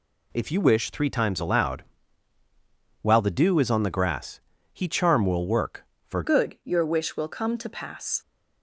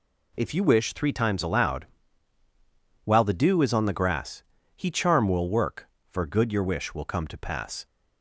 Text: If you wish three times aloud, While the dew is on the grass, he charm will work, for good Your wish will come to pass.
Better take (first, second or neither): second